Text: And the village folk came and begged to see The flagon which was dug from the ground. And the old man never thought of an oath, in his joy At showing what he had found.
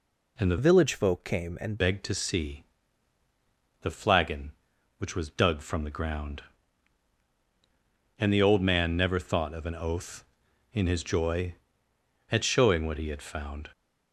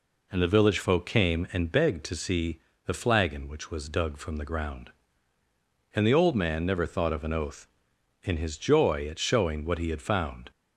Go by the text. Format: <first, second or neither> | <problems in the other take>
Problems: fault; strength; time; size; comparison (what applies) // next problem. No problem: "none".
second | changes voice from "village" to "and"; from 0.5 to 1.7 s; 1.2 s long // pauses between "see" and "The"; at 2.6 s; 1.1 s long; slight in the second